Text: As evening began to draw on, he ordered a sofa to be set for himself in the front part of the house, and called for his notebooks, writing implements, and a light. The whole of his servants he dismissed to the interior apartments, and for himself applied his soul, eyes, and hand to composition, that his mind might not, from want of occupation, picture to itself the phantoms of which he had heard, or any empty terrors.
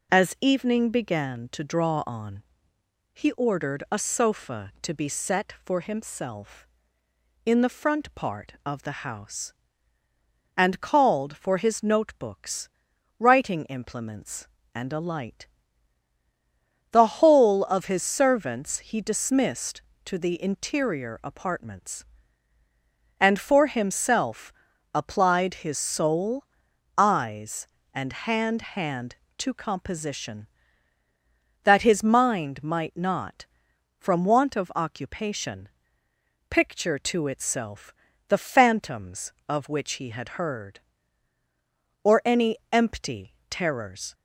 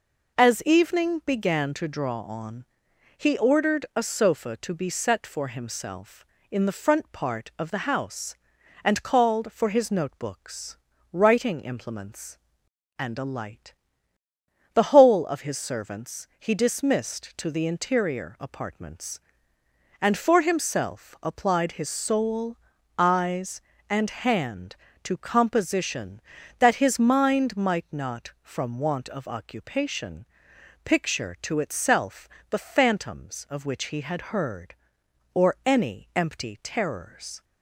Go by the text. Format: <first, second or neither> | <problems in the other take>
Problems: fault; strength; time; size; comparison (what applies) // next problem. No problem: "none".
second | pauses between "himself" and "applied"; at 24.5 s; 0.40 s long // says "hand" twice; at 28.6 s // pauses between "itself" and "the"; slight; at 37.9 s; 0.34 s long; slight in the second // pauses between "empty" and "terrors"; slight; at 43.3 s; 0.16 s long